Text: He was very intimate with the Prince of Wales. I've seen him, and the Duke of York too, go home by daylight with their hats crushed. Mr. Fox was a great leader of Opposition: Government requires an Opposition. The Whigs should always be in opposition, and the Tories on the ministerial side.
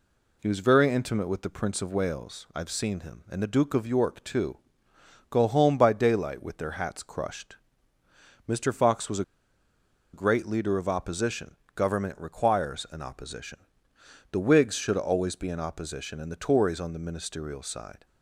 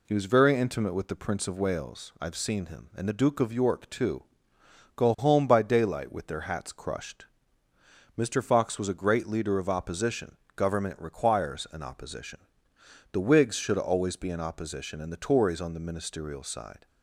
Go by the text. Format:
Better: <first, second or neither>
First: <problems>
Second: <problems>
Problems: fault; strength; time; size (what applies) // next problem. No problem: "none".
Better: second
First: pauses between "a" and "great"; noticeable; at 9.2 s; 0.88 s long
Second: none